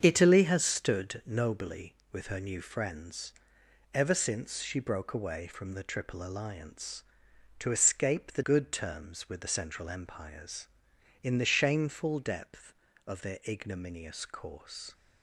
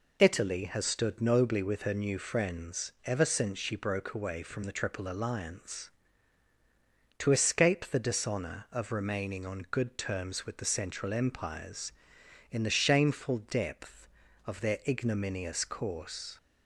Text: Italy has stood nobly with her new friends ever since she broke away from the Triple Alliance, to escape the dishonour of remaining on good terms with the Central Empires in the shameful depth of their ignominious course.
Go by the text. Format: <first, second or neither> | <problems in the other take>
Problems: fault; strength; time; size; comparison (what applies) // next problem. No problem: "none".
second | starts louder than the rest; strong; until 1.0 s; 7 dB // pauses between "friends" and "ever"; noticeable; at 3.3 s; 0.60 s long // skips "dishonour of remaining on"; at 8.4 s